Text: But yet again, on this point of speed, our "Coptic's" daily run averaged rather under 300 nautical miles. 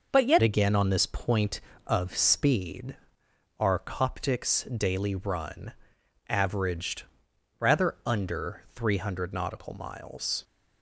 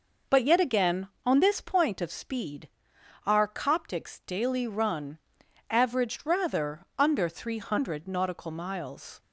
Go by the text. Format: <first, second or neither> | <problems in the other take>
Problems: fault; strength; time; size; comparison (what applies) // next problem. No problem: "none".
second | changes voice at "again"; from 0.4 s on; 10.0 s long // pauses between "run" and "averaged"; noticeable; at 5.7 s; 0.56 s long; noticeable in the second // pauses between "averaged" and "rather"; noticeable; at 7.0 s; 0.56 s long